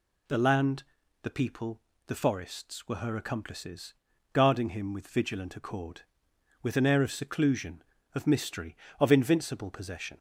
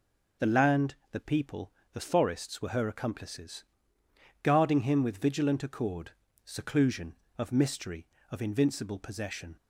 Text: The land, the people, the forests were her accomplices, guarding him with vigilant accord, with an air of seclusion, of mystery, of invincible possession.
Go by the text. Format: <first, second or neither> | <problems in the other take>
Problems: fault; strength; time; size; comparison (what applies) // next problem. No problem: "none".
first | skips "with an air of"; at 6.2 s